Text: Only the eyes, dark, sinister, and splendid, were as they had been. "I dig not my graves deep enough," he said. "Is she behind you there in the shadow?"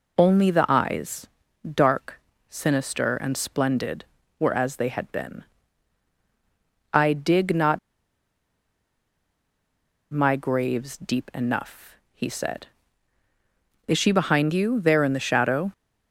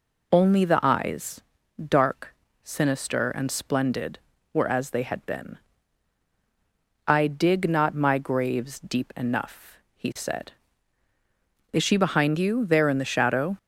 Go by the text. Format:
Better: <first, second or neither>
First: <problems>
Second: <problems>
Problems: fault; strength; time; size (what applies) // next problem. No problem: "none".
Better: second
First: pauses between "not" and "my"; strong; at 7.7 s; 2.3 s long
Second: none